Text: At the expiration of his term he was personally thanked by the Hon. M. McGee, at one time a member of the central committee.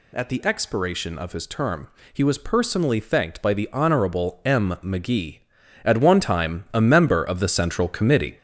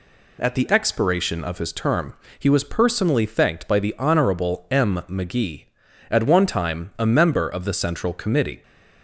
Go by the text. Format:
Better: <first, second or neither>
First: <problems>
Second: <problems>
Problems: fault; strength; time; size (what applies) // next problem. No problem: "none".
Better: second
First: gets louder; noticeable; throughout; 5.5 dB // pauses between "term" and "he"; slight; at 1.8 s; 0.24 s long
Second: pauses between "term" and "he"; slight; at 2.1 s; 0.24 s long